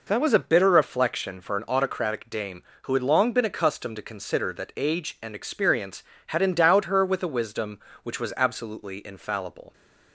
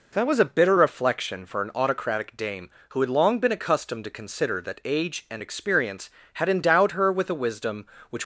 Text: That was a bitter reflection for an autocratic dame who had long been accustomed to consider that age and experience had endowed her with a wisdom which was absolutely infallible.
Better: first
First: none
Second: stops before "was absolutely infallible"; at 8.2 s

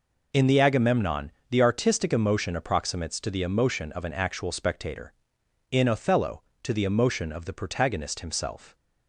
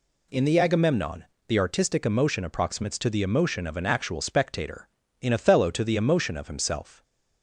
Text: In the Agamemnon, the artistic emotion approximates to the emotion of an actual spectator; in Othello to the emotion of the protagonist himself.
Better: first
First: none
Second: skips "the protagonist"; at 6.4 s

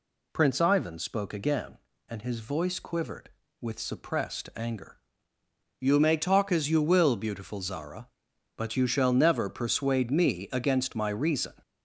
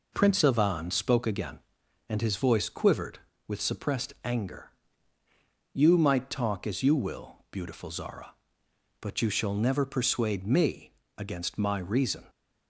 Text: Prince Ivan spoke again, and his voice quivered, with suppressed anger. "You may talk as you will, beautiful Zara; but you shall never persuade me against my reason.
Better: first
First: none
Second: says "might" for "may"; at 5.9 s // pauses between "me" and "against"; slight; at 10.9 s; 0.26 s long

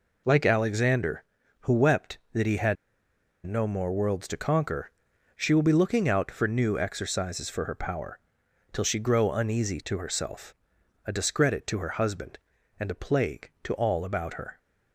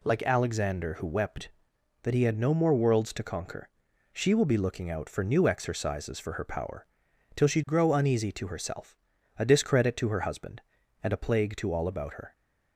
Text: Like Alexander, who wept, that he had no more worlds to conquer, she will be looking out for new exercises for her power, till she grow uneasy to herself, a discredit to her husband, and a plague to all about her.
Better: second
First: pauses between "had" and "no"; noticeable; at 2.7 s; 0.70 s long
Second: none

